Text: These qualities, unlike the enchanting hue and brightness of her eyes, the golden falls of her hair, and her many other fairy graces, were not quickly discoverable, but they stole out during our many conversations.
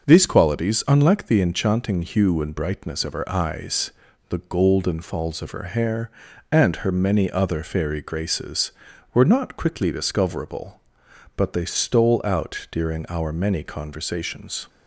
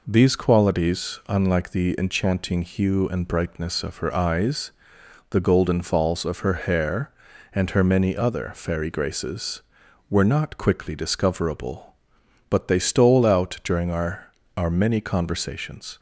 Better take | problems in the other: first | says "our" twice; at 14.5 s

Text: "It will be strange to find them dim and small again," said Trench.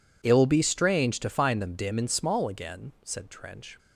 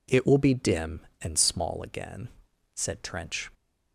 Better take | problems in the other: first | skips "strange to find them"; at 0.5 s

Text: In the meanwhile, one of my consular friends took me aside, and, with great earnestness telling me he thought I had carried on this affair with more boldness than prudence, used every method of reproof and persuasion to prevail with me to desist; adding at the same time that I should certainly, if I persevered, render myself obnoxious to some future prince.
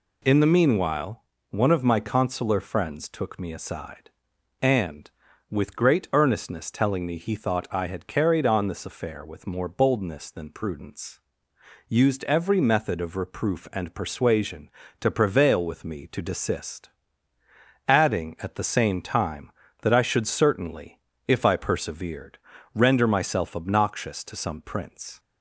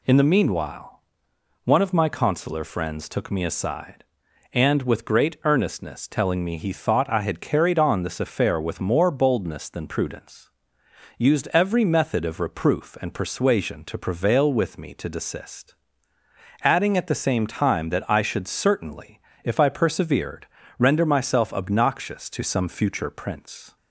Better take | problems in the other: second | skips "future"; at 24.6 s

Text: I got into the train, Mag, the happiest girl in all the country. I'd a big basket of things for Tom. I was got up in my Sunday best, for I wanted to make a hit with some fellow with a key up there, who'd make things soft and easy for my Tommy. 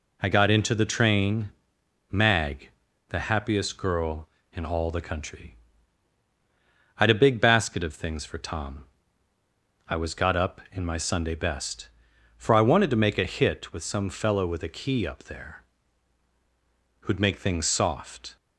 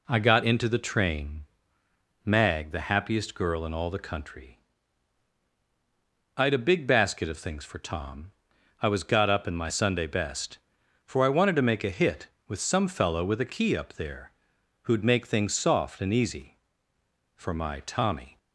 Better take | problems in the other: second | stops before "and easy for my Tommy"; at 18.3 s

